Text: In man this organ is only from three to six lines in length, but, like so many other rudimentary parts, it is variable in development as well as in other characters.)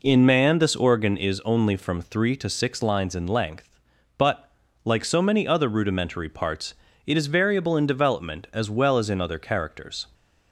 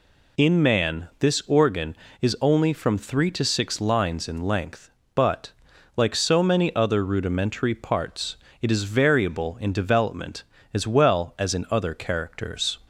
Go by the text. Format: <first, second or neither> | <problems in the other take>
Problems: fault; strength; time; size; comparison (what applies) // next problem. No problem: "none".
second | starts louder than the rest; noticeable; until 1.1 s; 4 dB